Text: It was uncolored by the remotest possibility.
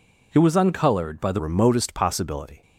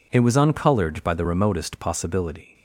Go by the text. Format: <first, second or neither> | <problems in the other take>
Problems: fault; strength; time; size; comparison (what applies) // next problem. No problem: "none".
second | changes voice at "remotest"; from 1.3 s on; 1.3 s long